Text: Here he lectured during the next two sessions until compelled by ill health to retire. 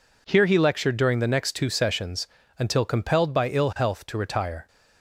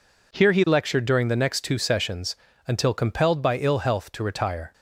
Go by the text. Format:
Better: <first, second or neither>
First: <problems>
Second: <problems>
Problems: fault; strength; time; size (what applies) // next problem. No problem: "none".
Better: neither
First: pauses between "sessions" and "until"; slight; at 2.2 s; 0.32 s long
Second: pauses between "sessions" and "until"; slight; at 2.3 s; 0.32 s long